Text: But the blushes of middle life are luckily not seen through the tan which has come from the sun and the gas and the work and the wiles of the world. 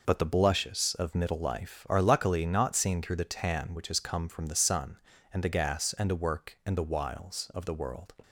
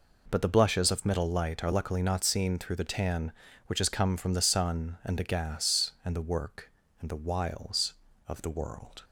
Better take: first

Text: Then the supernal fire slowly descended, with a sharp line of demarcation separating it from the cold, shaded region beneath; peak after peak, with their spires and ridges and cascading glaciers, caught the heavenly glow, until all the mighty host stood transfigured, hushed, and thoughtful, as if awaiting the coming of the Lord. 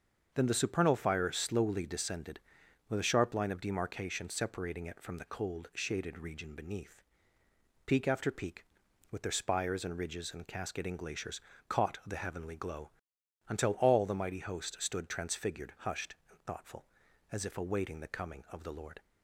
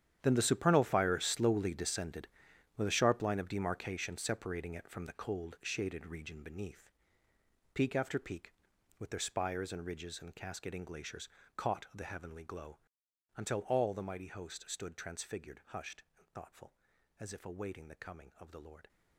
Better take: first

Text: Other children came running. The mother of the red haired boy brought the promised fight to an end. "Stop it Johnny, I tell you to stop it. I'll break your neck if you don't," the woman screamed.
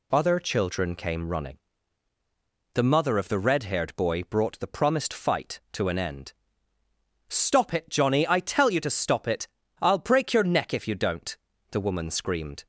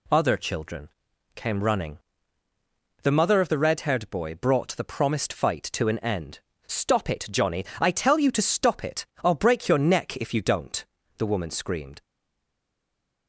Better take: first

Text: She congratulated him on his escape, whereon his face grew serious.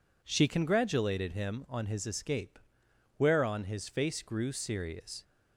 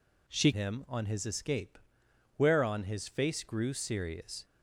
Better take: first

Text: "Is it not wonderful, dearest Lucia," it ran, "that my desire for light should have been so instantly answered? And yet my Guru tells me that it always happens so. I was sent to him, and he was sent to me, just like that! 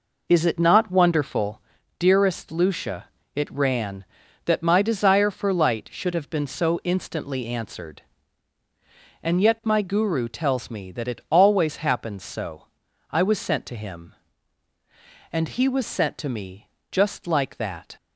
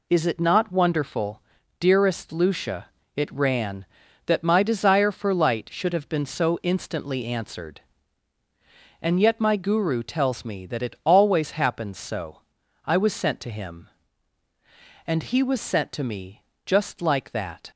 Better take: second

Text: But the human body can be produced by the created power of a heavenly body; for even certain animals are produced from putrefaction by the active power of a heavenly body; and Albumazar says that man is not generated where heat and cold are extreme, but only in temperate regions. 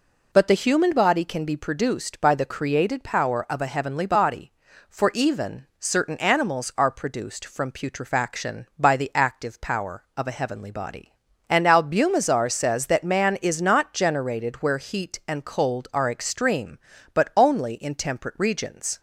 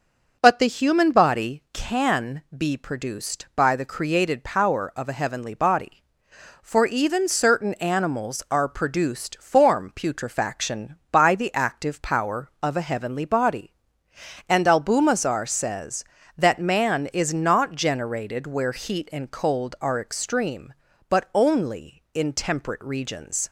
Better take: first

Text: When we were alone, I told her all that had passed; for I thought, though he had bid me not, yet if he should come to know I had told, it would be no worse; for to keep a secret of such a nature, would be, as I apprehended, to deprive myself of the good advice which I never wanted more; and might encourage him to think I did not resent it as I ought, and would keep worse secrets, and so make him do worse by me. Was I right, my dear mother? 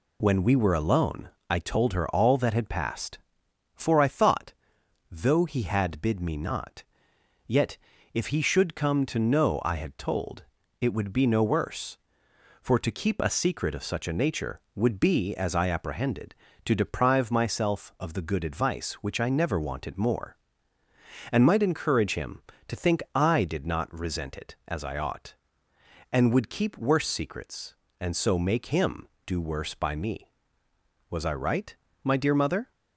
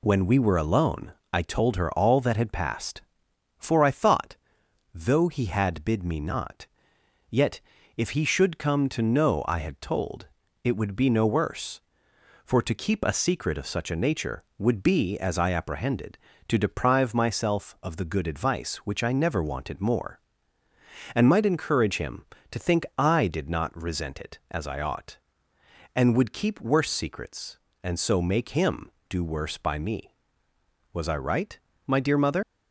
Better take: first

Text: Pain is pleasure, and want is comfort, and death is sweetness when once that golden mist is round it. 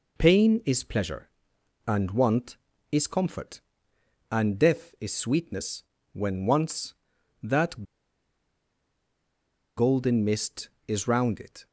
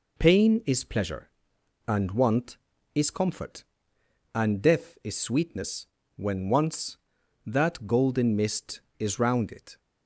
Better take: second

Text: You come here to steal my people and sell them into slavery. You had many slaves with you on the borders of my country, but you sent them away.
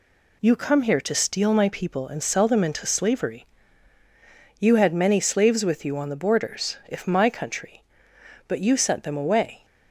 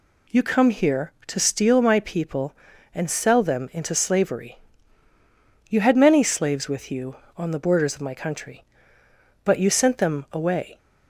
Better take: second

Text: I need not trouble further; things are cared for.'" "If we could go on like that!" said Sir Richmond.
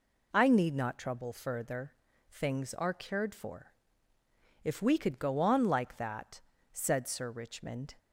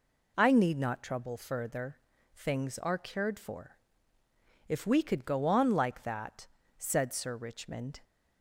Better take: neither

